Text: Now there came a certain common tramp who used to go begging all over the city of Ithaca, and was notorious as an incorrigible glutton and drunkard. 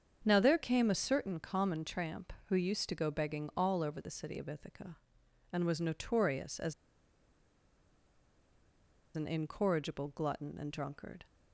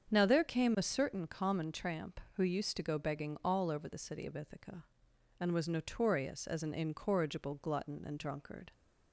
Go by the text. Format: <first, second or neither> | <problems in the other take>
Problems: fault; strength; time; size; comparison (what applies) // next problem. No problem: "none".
second | starts louder than the rest; strong; until 1.2 s; 7.5 dB; strong in the second // pauses between "as" and "an"; strong; at 6.7 s; 2.4 s long